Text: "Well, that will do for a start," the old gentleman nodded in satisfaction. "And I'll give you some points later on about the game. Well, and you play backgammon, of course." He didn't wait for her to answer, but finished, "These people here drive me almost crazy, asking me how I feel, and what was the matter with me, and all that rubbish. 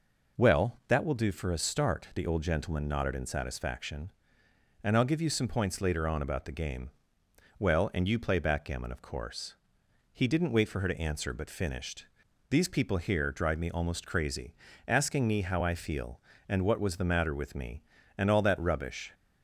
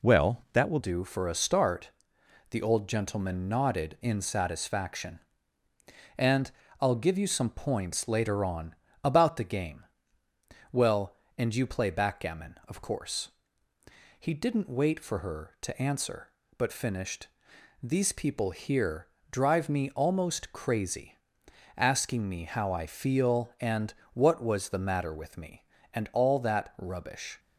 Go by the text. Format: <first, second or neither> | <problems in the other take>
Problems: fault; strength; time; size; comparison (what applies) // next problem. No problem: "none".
first | changes voice at "do"; from 0.7 s on; 26.6 s long // pauses between "And" and "I'll"; slight; at 6.5 s; 0.30 s long // pauses between "on" and "about"; slight; at 8.7 s; 0.26 s long // pauses between "here" and "drive"; slight; at 19.0 s; 0.24 s long // pauses between "and" and "what"; slight; at 23.9 s; 0.22 s long